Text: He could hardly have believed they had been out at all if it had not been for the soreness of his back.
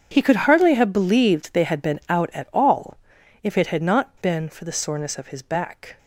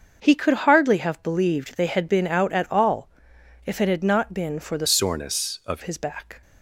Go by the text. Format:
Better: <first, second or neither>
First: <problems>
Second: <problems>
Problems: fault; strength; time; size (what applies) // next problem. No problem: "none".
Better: first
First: starts louder than the rest; strong; until 1.1 s; 7.5 dB // pauses between "all" and "if"; at 2.9 s; 0.44 s long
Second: starts louder than the rest; until 1.2 s; 6.5 dB // pauses between "all" and "if"; noticeable; at 3.0 s; 0.56 s long // changes voice from "soreness" to "of"; from 4.8 to 5.8 s; 1.0 s long